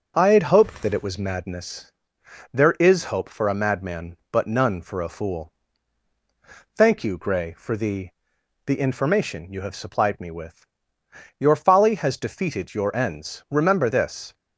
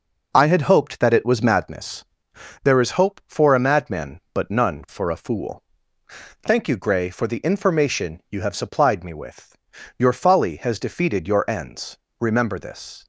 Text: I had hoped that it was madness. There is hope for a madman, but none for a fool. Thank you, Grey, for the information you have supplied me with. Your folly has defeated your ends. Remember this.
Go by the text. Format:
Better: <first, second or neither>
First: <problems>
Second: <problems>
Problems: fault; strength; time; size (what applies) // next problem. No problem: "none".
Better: second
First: says "the" twice; at 8.6 s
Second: none